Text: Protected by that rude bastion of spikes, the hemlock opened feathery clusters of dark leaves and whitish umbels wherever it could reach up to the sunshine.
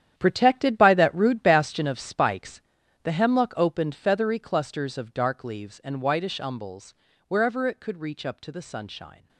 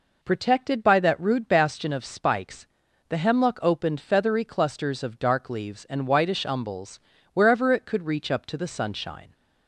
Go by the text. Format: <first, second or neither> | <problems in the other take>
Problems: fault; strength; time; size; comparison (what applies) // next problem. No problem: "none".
second | gets quieter; strong; throughout; 13 dB // pauses between "umbels" and "wherever"; slight; at 6.9 s; 0.34 s long; slight in the second